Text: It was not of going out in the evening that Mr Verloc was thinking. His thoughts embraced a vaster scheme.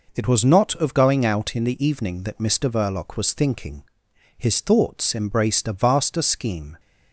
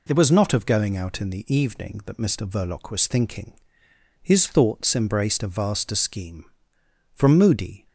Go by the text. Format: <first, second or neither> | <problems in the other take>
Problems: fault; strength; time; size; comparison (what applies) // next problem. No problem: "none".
first | goes on to say "From moody"; noticeable; from 7.1 s on; 0.74 s long